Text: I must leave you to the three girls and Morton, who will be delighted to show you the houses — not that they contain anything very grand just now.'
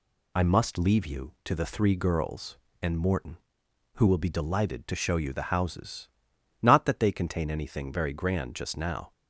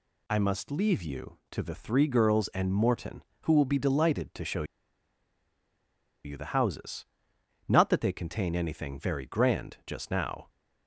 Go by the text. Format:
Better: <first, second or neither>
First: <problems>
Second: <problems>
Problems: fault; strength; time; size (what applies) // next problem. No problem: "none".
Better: first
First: none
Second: pauses between "show" and "you"; strong; at 4.6 s; 1.6 s long